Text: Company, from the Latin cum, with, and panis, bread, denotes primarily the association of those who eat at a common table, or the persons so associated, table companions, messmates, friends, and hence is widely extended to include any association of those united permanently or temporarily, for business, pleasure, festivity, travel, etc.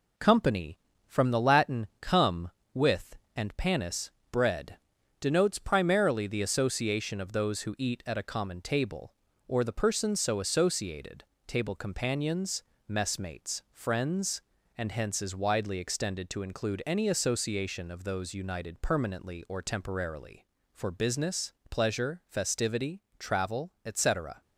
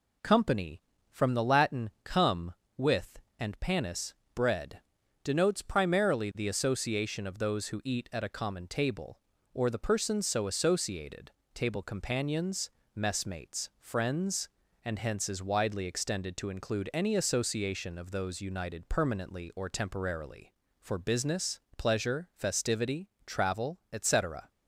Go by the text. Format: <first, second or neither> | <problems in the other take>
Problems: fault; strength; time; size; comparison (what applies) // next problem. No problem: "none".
second | gets quieter; slight; throughout; 3.5 dB